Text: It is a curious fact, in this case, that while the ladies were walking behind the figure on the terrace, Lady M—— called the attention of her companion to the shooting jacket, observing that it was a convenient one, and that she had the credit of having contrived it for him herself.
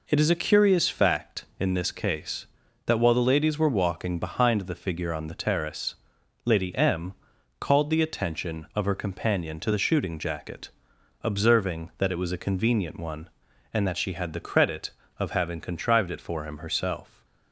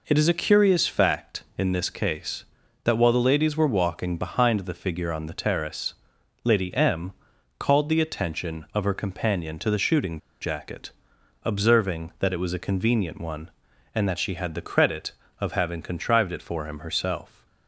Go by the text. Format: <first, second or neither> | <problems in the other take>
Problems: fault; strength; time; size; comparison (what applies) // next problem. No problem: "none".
first | pauses between "shooting" and "jacket"; slight; at 10.1 s; 0.22 s long